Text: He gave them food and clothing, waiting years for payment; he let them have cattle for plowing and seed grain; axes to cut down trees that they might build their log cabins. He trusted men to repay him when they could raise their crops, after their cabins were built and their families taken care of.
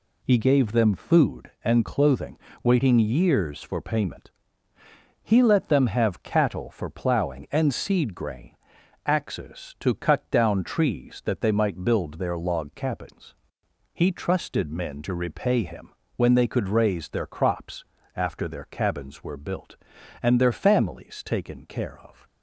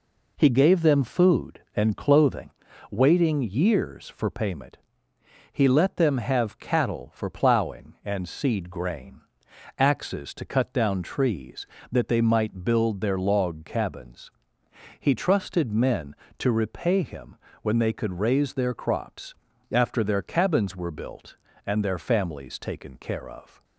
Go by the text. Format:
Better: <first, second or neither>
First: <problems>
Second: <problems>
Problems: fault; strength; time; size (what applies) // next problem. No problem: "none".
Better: neither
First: pauses between "him" and "when"; slight; at 15.8 s; 0.26 s long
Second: pauses between "him" and "when"; slight; at 17.3 s; 0.24 s long